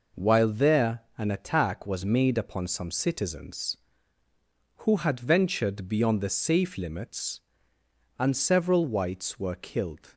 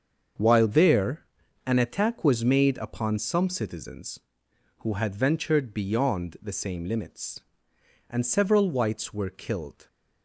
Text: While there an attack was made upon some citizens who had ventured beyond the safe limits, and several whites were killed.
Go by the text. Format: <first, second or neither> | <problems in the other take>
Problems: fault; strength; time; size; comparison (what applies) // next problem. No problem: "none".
first | starts louder than the rest; until 1.7 s; 6.5 dB // pauses between "there" and "an"; at 1.2 s; 0.40 s long; slight in the first // says "same" for "safe"; at 6.5 s